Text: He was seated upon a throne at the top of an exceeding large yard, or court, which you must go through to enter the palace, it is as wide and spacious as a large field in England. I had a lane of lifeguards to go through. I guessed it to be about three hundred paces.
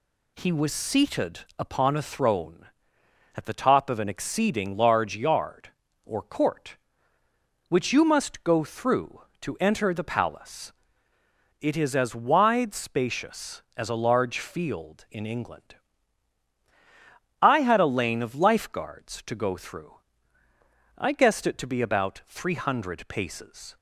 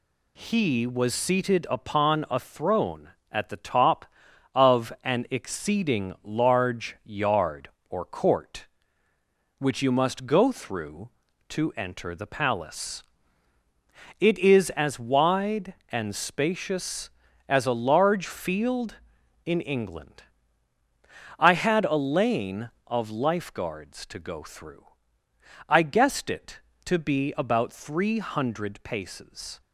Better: second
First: pauses between "seated" and "upon"; slight; at 1.4 s; 0.18 s long // skips "and"; at 12.7 s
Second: none

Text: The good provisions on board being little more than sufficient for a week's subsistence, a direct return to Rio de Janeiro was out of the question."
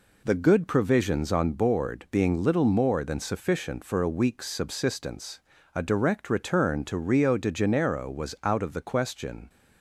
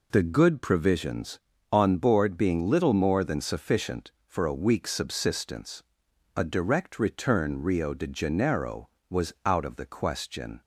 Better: first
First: none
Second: skips "to"; at 7.6 s

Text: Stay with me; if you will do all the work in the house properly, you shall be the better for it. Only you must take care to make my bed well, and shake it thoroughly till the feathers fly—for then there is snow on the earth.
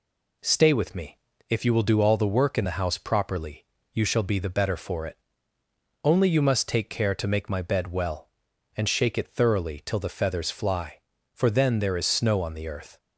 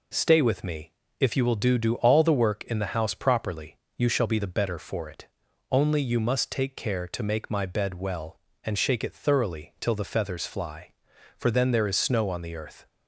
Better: first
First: none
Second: says "do" twice; at 1.7 s

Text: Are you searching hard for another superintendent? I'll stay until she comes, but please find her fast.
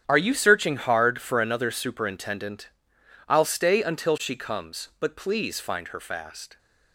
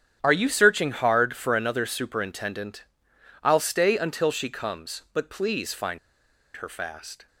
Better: first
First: starts louder than the rest; strong; until 1.0 s; 9 dB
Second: starts louder than the rest; strong; until 1.2 s; 9 dB // pauses between "find" and "her"; noticeable; at 5.9 s; 0.57 s long

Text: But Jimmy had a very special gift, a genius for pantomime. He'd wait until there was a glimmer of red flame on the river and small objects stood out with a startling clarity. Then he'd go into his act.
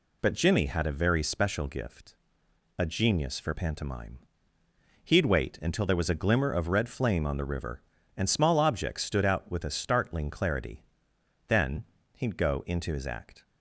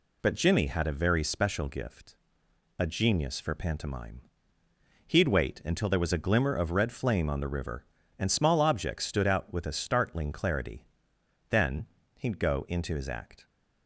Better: neither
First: pauses between "Then" and "he'd"; slight; at 11.8 s; 0.34 s long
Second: pauses between "Then" and "he'd"; slight; at 11.8 s; 0.34 s long

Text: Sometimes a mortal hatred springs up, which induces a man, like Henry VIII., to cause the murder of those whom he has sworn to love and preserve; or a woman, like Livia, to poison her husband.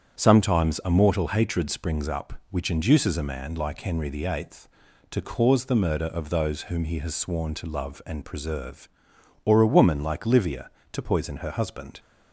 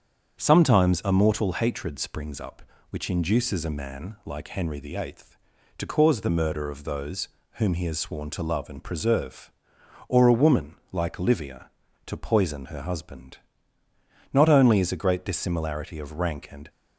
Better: first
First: starts louder than the rest; strong; until 1.2 s; 8.5 dB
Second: starts louder than the rest; strong; until 1.4 s; 7.5 dB // pauses between "those" and "whom"; slight; at 7.2 s; 0.26 s long // goes on to say "Not only is a great dissimilarity of rank and"; strong; from 14.3 s on; 2.3 s long

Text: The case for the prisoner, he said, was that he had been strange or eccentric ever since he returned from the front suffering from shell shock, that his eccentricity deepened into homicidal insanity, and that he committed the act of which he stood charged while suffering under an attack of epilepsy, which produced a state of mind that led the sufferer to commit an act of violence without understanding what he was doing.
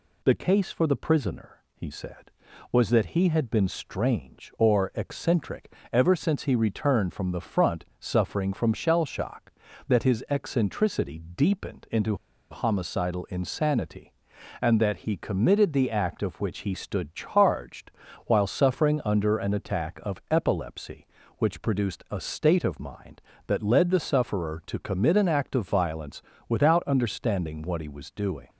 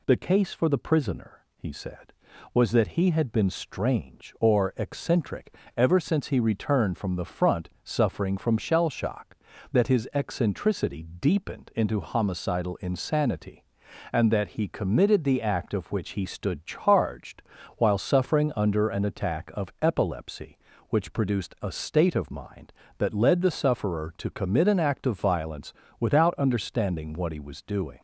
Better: second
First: pauses between "eccentric" and "ever"; slight; at 5.7 s; 0.20 s long // pauses between "into" and "homicidal"; slight; at 12.1 s; 0.34 s long // pauses between "charged" and "while"; at 17.8 s; 0.38 s long // pauses between "violence" and "without"; slight; at 26.2 s; 0.26 s long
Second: pauses between "eccentric" and "ever"; slight; at 5.5 s; 0.22 s long // pauses between "charged" and "while"; at 17.4 s; 0.38 s long // pauses between "violence" and "without"; slight; at 25.7 s; 0.26 s long

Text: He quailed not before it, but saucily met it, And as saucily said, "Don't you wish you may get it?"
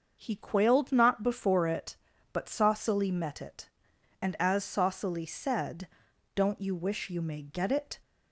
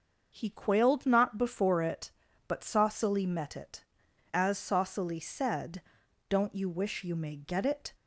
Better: first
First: starts louder than the rest; until 1.2 s; 6.5 dB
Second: starts louder than the rest; until 1.3 s; 6 dB // skips "And"; at 4.0 s

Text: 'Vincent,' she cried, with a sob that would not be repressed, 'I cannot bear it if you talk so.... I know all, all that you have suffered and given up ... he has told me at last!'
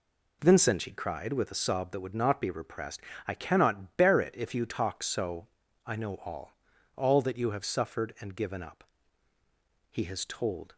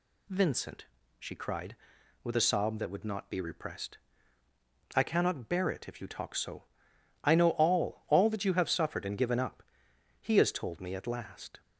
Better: second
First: stops before "me at last"; at 10.7 s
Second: none

